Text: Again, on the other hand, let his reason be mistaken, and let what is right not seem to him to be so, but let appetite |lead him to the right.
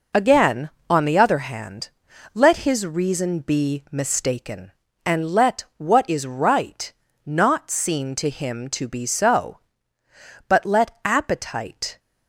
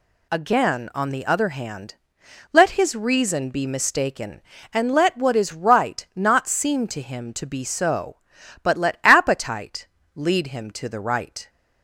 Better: second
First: pauses between "right" and "not"; slight; at 6.9 s; 0.32 s long // stops before "lead him to the right"; at 11.9 s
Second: none

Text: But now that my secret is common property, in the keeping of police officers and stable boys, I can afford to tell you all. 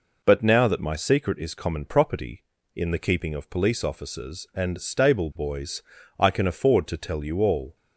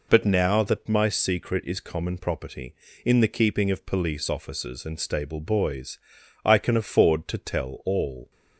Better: first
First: none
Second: skips "you"; at 7.8 s

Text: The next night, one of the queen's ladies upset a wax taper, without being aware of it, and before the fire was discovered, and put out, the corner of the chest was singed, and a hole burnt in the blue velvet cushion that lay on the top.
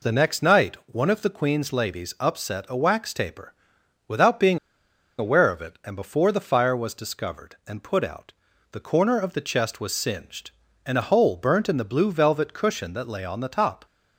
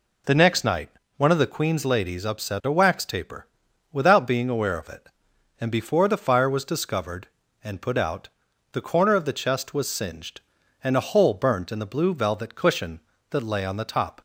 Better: second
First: pauses between "being" and "aware"; noticeable; at 4.5 s; 0.60 s long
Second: none

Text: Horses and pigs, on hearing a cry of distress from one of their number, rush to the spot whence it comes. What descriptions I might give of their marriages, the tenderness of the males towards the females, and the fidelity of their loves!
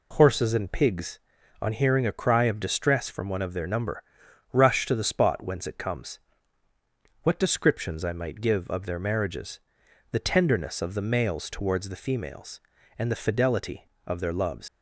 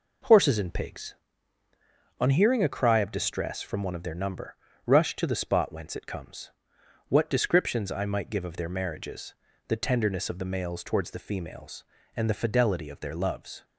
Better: second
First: leaves "loves" unfinished; at 14.6 s; 135 ms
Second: none

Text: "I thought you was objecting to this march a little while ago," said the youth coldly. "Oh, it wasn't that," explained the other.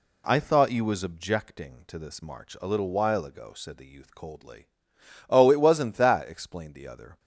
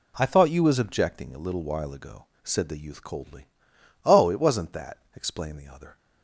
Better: first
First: none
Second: skips "to this march"; at 1.3 s

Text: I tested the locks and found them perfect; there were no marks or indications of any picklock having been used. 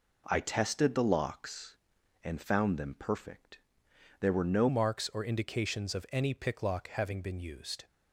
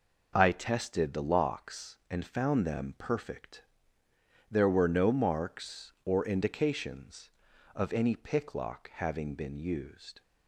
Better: second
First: changes voice at "marks"; from 4.6 s on; 3.2 s long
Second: none

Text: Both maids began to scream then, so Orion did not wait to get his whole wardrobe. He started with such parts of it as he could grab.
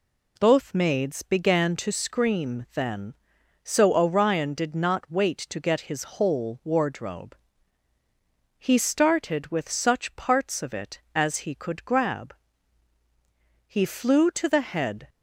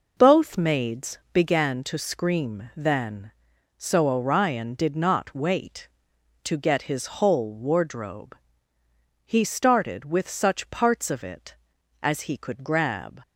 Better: second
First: goes on to say "He flew to the head"; from 13.6 s on; 1.4 s long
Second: none

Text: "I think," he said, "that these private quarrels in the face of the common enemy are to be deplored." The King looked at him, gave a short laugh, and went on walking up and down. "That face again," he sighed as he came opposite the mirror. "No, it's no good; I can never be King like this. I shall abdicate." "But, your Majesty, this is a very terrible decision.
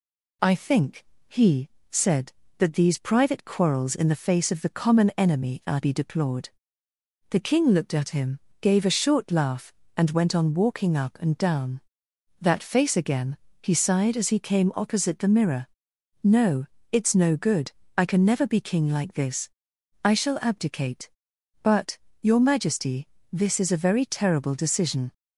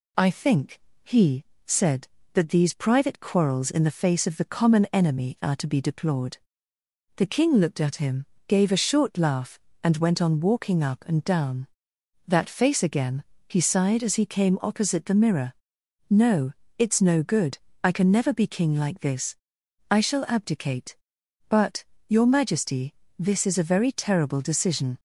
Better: second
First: pauses between "he" and "said"; slight; at 1.6 s; 0.20 s long // skips "to"; at 5.8 s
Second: pauses between "he" and "said"; slight; at 1.4 s; 0.20 s long

